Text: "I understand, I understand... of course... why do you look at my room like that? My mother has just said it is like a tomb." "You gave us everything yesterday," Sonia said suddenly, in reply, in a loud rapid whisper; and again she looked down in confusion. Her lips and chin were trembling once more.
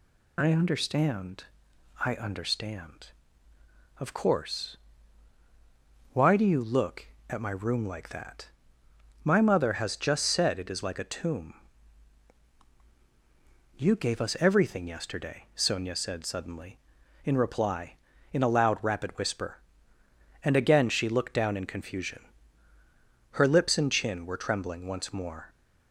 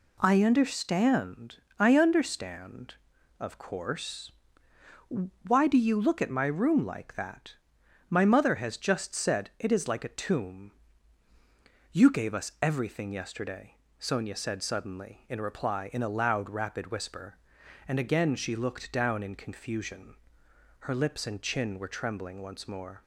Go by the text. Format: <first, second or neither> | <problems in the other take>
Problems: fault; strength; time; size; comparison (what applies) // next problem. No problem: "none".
neither | none